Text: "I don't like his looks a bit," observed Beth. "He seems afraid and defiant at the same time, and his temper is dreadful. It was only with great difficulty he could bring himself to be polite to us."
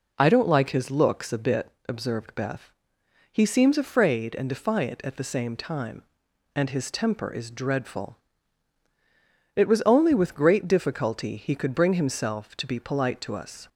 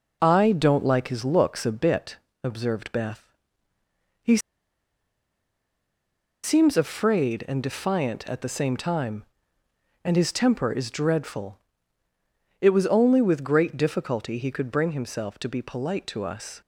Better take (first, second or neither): first